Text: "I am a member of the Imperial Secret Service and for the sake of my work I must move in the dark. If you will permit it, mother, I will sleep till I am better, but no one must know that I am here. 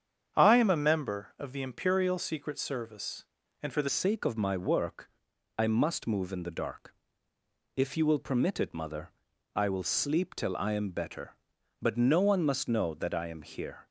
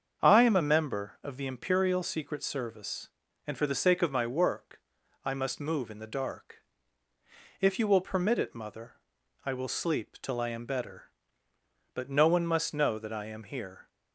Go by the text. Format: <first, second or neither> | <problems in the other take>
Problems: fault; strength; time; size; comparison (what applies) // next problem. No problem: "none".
second | starts louder than the rest; strong; until 1.4 s; 8 dB; also in the second // changes voice at "sake"; from 3.8 s on; 10.0 s long // pauses between "work" and "I"; noticeable; at 5.0 s; 0.48 s long; noticeable in the second